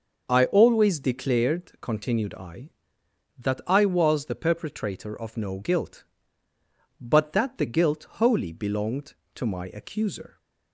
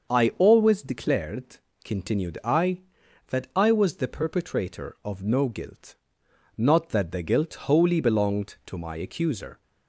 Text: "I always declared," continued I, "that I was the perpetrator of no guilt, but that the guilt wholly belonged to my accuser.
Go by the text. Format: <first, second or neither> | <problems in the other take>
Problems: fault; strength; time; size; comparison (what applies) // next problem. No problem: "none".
first | starts louder than the rest; until 1.1 s; 6.5 dB; also in the first // says "not" for "but"; at 6.5 s